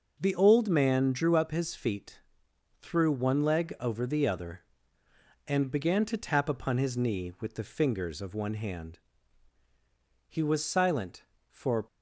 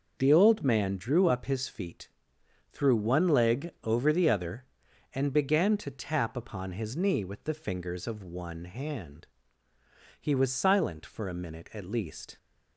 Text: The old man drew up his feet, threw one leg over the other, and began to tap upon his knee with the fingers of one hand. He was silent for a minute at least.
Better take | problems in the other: second | stops before "a minute at least"; at 11.8 s

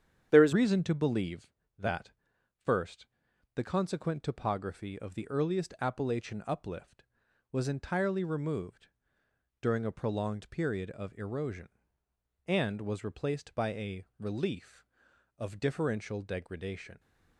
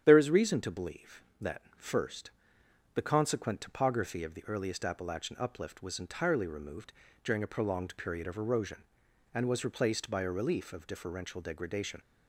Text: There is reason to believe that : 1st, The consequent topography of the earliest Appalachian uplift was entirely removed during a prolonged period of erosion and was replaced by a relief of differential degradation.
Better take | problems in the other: second | starts louder than the rest; strong; until 1.3 s; 9 dB; strong in the second // changes voice at "reason"; from 0.5 s on; 16.4 s long // pauses between "removed" and "during"; noticeable; at 8.8 s; 0.74 s long; slight in the second

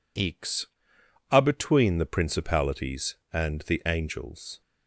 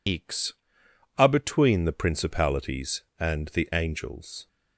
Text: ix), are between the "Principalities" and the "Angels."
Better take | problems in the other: first | loses the start of "ix"; at 0.0 s; 40 ms

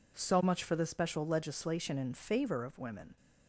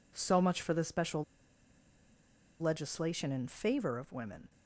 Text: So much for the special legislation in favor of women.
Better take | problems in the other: first | pauses between "special" and "legislation"; strong; at 1.2 s; 1.3 s long

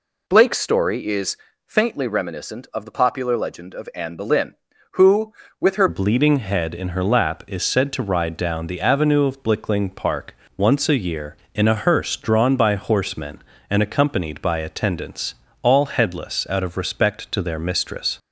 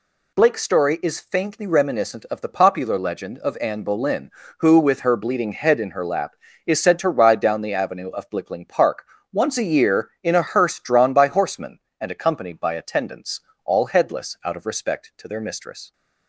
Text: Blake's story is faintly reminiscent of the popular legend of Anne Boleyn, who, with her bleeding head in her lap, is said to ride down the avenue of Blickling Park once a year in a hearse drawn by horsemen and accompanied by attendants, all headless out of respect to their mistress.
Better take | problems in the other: second | pauses between "is" and "faintly"; slight; at 1.3 s; 0.28 s long // changes voice at "bleeding"; from 5.8 s on; 12.3 s long // pauses between "Park" and "once"; slight; at 10.3 s; 0.22 s long; slight in the second

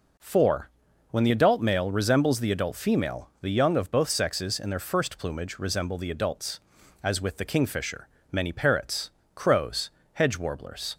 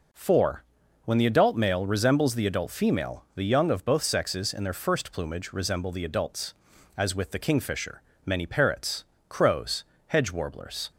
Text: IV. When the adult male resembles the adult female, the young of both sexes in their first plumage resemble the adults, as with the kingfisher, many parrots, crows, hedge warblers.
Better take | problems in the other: neither | none

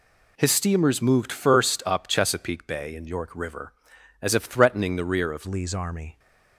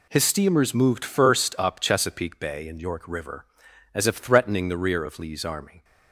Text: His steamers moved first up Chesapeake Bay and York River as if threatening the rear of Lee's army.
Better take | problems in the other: second | changes voice at "Lee's"; from 5.4 s on; 0.7 s long

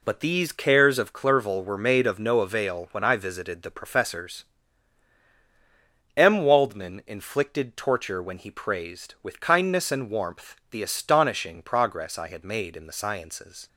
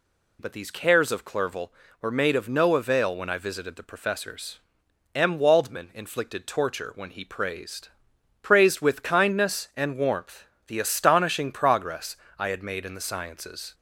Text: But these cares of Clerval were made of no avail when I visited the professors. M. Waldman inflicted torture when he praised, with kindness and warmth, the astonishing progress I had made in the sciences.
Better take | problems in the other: first | says "praised" twice; at 8.4 s // pauses between "progress" and "I"; slight; at 12.1 s; 0.22 s long

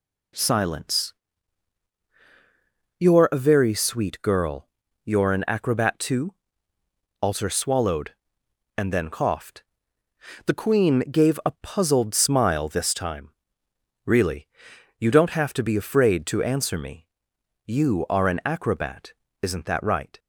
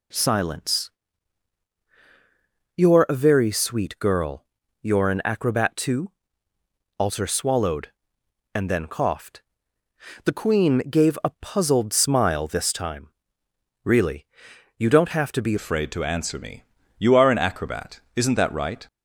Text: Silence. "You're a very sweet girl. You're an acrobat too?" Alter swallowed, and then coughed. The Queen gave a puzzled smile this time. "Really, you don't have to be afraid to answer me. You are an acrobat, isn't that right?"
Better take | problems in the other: first | changes voice at "afraid"; from 15.5 s on; 3.3 s long

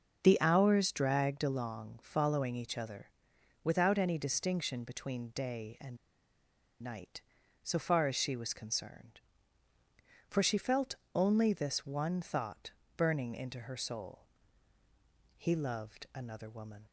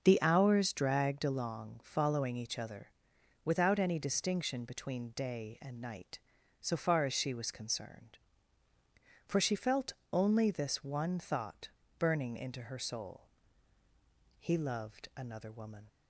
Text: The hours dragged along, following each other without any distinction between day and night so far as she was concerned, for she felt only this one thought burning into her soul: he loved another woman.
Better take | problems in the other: second | starts louder than the rest; until 1.2 s; 6 dB; also in the second // pauses between "other" and "without"; noticeable; at 3.0 s; 0.56 s long; noticeable in the second // pauses between "and" and "night"; noticeable; at 5.9 s; 0.86 s long // pauses between "felt" and "only"; slight; at 10.9 s; 0.18 s long; slight in the second // pauses between "thought" and "burning"; slight; at 12.7 s; 0.24 s long; slight in the second

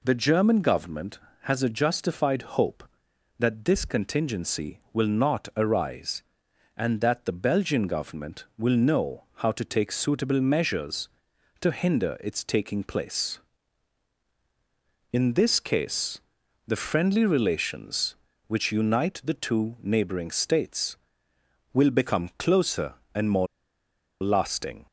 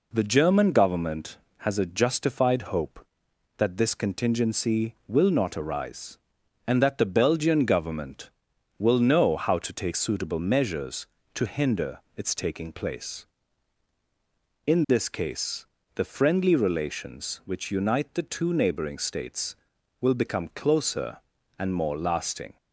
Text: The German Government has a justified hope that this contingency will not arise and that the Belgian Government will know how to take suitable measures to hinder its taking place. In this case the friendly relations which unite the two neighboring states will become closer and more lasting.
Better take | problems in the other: second | pauses between "case" and "the"; noticeable; at 16.1 s; 0.46 s long; slight in the second // pauses between "more" and "lasting"; noticeable; at 23.4 s; 0.75 s long

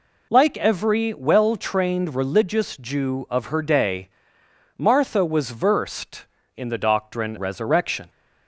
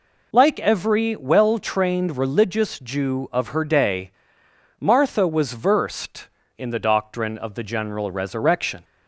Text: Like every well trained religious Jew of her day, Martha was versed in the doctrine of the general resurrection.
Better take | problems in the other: second | skips "of the general"; at 7.3 s

